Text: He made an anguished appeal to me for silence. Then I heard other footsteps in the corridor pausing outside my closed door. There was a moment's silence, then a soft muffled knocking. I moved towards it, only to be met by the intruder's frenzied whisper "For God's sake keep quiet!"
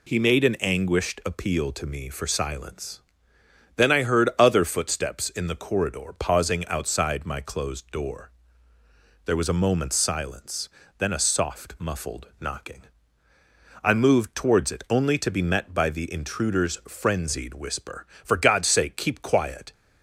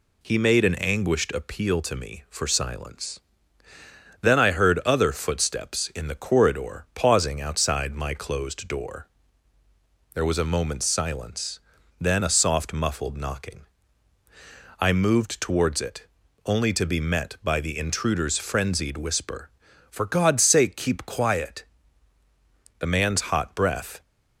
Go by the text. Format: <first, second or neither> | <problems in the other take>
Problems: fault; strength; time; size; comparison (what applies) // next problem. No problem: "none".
first | goes on to say "The man's hot breath"; noticeable; from 22.7 s on; 1.2 s long